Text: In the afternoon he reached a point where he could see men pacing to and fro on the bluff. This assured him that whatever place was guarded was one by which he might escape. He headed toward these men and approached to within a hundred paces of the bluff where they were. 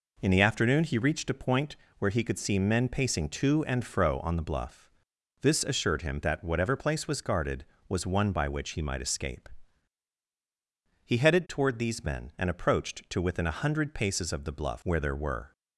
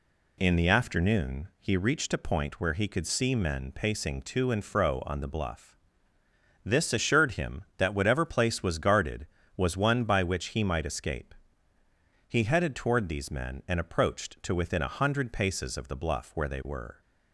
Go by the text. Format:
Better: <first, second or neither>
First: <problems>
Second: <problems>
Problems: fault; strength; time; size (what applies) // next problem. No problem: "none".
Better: second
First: pauses between "point" and "where"; slight; at 1.7 s; 0.24 s long // says "there" for "they"; at 15.0 s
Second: none